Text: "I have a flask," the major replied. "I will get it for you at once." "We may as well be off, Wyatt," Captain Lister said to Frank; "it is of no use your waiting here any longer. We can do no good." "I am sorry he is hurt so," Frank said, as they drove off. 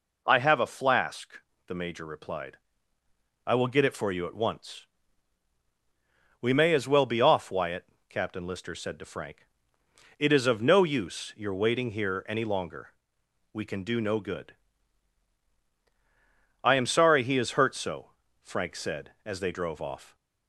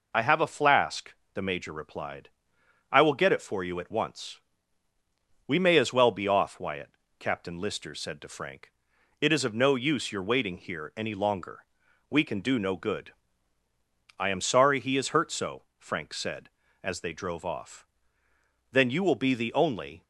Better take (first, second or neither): first